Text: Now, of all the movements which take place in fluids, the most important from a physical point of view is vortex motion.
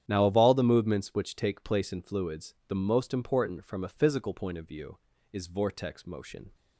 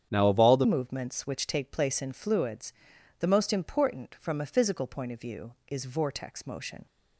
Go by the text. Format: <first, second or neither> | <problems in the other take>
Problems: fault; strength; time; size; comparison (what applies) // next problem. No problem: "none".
first | starts louder than the rest; strong; until 1.1 s; 8.5 dB; strong in the first // changes voice at "movements"; from 0.6 s on; 6.2 s long